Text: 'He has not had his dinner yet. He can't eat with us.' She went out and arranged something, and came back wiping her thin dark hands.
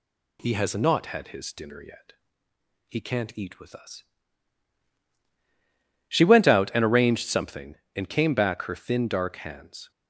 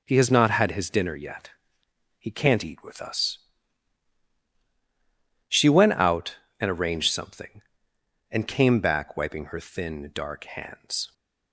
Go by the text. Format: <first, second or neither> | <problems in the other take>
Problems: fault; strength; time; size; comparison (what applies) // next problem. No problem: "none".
second | skips "wiping"; at 8.6 s